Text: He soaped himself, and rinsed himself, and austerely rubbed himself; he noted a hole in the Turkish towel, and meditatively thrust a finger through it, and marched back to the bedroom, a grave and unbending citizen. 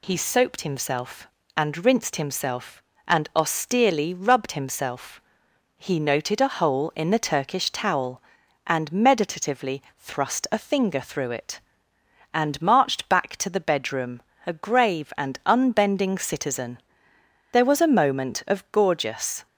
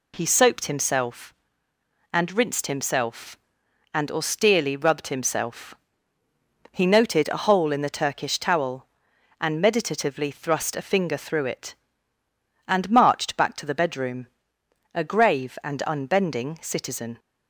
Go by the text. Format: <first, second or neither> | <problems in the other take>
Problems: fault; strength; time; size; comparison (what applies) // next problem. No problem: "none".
second | goes on to say "There was a moment of gorgeous"; strong; from 17.5 s on; 1.9 s long